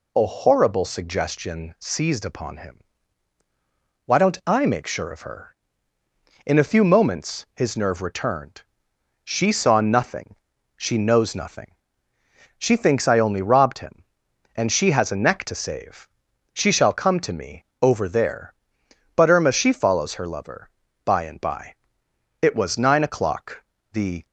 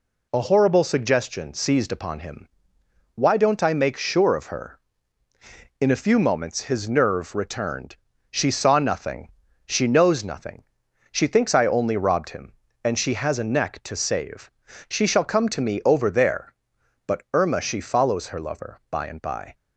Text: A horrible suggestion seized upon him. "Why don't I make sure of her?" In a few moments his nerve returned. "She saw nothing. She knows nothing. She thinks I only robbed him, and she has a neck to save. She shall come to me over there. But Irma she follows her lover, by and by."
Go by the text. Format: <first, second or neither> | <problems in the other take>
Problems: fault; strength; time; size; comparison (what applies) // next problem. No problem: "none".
second | pauses between "me" and "over"; slight; at 17.6 s; 0.18 s long // goes on to say "It was nine o'clock the"; strong; from 22.4 s on; 1.8 s long